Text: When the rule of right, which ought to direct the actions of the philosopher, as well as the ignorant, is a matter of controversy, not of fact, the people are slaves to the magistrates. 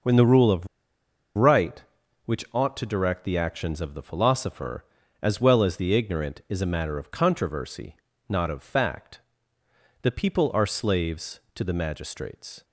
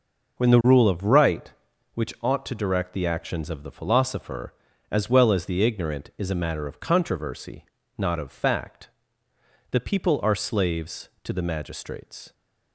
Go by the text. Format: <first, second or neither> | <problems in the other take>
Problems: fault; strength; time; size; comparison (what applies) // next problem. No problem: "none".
second | pauses between "of" and "right"; noticeable; at 0.6 s; 0.68 s long